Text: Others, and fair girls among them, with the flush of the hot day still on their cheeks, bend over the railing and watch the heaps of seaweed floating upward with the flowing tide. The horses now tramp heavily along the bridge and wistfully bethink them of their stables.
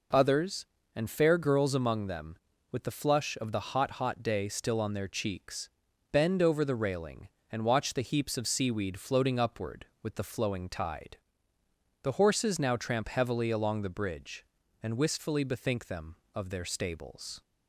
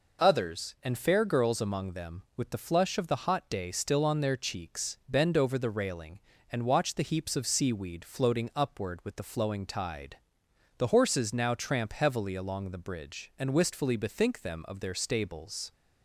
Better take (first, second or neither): second